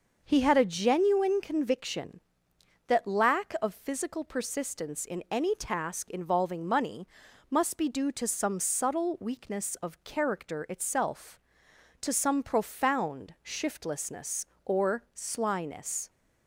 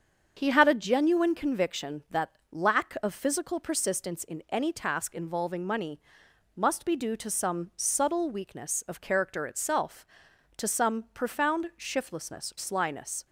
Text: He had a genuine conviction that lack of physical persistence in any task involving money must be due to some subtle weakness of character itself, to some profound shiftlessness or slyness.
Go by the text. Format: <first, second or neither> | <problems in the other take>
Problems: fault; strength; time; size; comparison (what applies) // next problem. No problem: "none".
first | starts louder than the rest; until 1.3 s; 7 dB; noticeable in the first // pauses between "that" and "lack"; slight; at 2.2 s; 0.22 s long // pauses between "money" and "must"; noticeable; at 5.9 s; 0.56 s long; also in the first // skips "or"; at 12.5 s